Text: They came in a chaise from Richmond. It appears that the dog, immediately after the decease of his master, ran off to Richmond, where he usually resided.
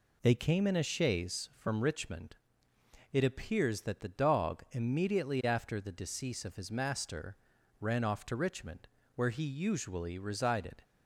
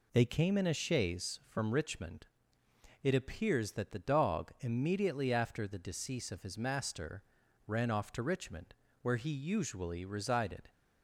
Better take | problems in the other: neither | none

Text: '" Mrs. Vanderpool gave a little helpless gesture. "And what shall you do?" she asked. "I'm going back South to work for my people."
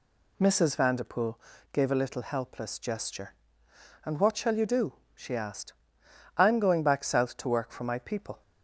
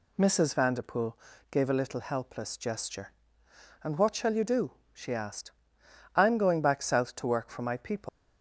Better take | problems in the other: first | pauses between "Vanderpool" and "gave"; slight; at 1.1 s; 0.32 s long; slight in the first // leaves "people" unfinished; at 8.0 s; 115 ms

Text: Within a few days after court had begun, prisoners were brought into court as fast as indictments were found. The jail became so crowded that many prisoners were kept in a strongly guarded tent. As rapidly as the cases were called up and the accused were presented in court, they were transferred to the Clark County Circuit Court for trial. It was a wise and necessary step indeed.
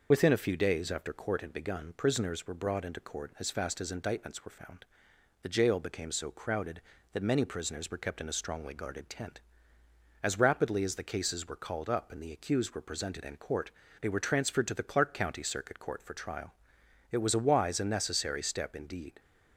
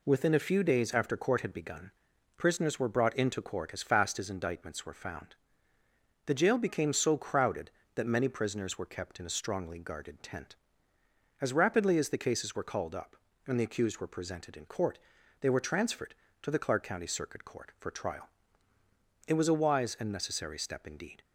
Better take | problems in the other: second | loses the start of "Within"; at 0.1 s; 55 ms

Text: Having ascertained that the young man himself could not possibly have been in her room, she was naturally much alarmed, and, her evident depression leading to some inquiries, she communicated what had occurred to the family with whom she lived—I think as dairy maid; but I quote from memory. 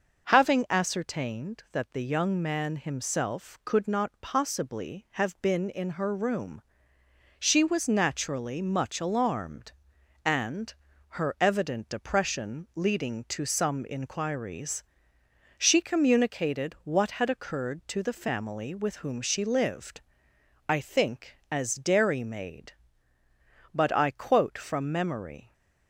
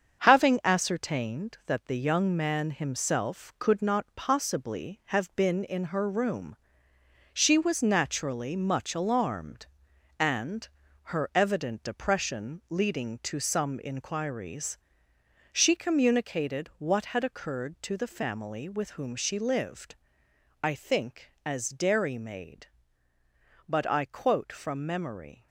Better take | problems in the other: first | gets quieter; throughout; 7 dB

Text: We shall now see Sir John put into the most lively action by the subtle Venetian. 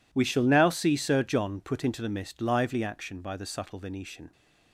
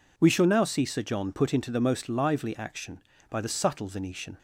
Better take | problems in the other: second | says "mist" for "most"; at 2.0 s

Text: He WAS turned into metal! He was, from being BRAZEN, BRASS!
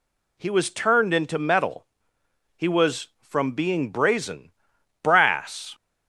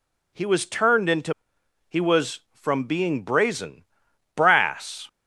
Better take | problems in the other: first | skips "metal"; at 1.5 s

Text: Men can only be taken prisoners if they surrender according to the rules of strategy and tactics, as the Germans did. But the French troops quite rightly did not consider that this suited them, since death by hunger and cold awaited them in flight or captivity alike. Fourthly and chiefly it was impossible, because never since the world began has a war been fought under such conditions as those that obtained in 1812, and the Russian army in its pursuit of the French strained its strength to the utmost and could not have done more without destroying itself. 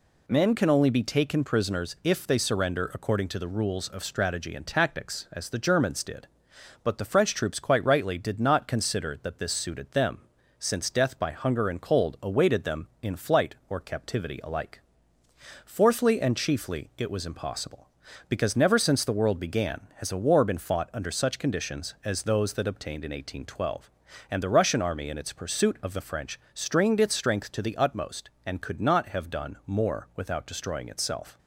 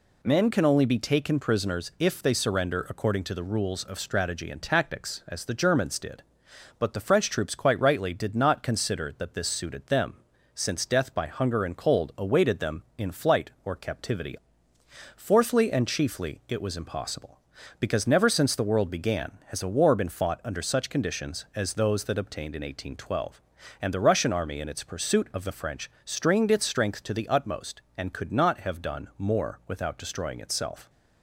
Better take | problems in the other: first | skips "alike"; at 14.7 s // pauses between "French" and "strained"; slight; at 25.8 s; 0.16 s long; slight in the first

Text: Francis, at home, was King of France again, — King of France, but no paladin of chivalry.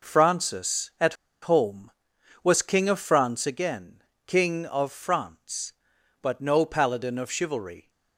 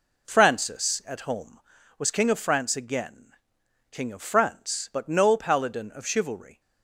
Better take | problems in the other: second | pauses between "at" and "home"; slight; at 1.1 s; 0.28 s long

